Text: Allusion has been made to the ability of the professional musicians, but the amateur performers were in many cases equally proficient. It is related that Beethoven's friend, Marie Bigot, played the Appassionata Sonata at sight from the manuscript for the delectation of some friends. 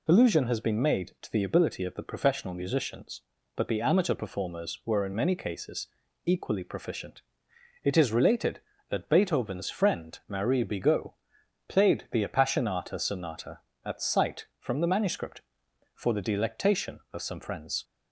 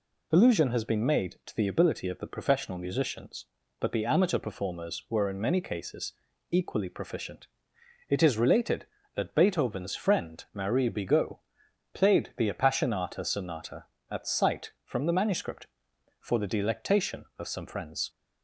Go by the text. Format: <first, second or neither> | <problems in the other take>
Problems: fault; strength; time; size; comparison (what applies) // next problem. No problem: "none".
neither | pauses between "cases" and "equally"; the same in both